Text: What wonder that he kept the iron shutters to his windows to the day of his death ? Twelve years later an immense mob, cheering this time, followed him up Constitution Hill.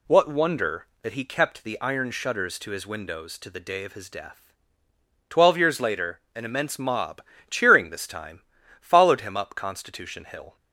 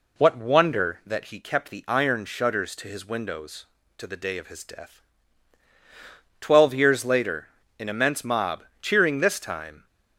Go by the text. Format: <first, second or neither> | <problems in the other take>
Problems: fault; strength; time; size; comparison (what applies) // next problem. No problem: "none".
first | pauses between "later" and "an"; slight; at 7.4 s; 0.30 s long; slight in the first // stops before "followed him up Constitution Hill"; at 9.8 s